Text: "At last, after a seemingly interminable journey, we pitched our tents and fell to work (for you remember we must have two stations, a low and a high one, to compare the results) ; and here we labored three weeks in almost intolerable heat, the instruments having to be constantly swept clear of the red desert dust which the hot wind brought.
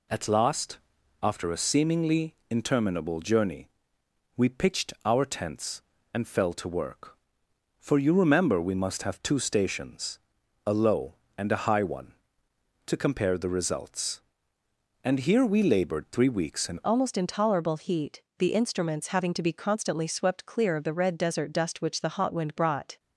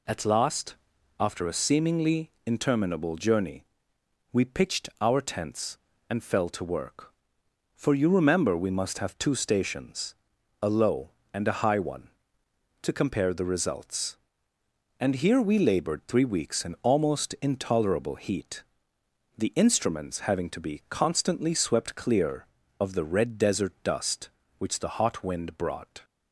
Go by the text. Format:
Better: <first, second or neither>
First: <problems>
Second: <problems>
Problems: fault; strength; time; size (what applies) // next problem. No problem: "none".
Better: second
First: pauses between "seemingly" and "interminable"; slight; at 2.3 s; 0.16 s long // changes voice at "almost"; from 16.8 s on; 6.1 s long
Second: pauses between "seemingly" and "interminable"; slight; at 2.3 s; 0.16 s long